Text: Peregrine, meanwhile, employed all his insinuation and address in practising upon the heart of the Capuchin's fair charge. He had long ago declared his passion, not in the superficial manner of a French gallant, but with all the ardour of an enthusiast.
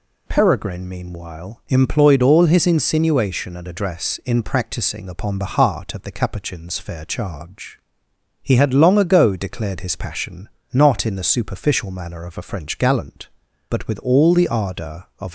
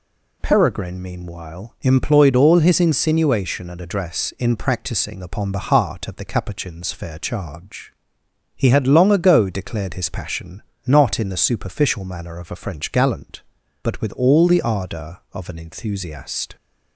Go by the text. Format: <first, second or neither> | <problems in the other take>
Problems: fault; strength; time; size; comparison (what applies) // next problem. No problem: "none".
second | stops before "an enthusiast"; at 15.2 s